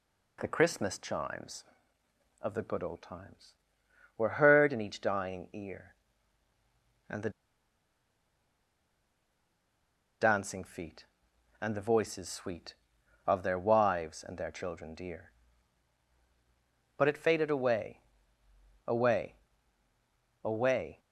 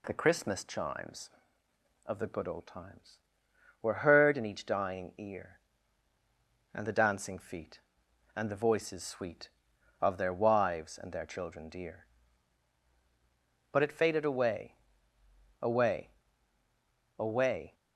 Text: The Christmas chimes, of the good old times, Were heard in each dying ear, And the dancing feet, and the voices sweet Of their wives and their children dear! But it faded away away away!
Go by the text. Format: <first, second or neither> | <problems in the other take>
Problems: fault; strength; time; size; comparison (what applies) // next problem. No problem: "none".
second | pauses between "the" and "dancing"; strong; at 7.2 s; 2.9 s long // pauses between "away" and "away"; noticeable; at 17.9 s; 0.88 s long; noticeable in the second // pauses between "away" and "away"; at 19.3 s; 1.1 s long; also in the second